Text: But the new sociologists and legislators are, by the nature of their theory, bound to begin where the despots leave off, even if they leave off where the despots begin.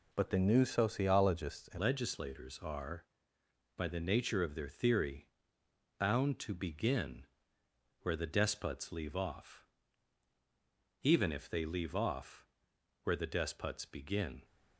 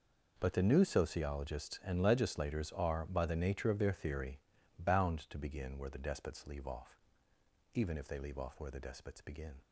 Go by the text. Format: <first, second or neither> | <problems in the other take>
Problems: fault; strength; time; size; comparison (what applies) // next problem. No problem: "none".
second | changes voice at "legislators"; from 1.7 s on; 12.7 s long // pauses between "begin" and "where"; noticeable; at 7.2 s; 0.74 s long // pauses between "off" and "where"; noticeable; at 12.4 s; 0.56 s long